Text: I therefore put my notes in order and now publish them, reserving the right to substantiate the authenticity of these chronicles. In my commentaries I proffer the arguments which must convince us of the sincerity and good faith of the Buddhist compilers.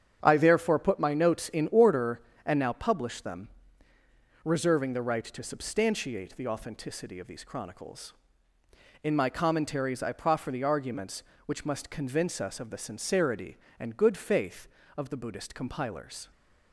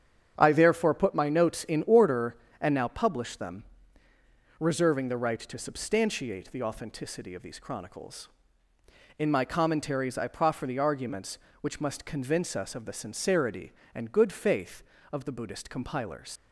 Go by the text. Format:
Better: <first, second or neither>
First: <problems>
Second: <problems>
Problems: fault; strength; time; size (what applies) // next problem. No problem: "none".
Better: first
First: starts louder than the rest; strong; until 1.2 s; 8 dB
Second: starts louder than the rest; strong; until 1.3 s; 8 dB // leaves "compilers" unfinished; at 16.3 s; 100 ms